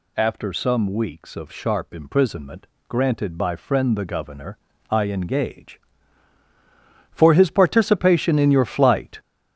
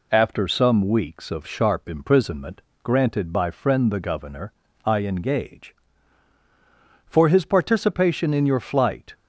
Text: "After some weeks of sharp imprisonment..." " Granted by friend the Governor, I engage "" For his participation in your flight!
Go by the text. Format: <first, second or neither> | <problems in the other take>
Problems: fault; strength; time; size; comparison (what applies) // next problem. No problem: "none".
second | gets louder; slight; throughout; 2.5 dB